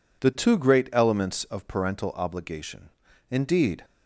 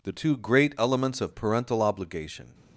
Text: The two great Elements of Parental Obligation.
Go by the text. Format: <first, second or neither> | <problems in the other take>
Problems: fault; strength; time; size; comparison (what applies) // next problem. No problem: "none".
second | goes on to say "Indeed"; from 3.3 s on; 0.54 s long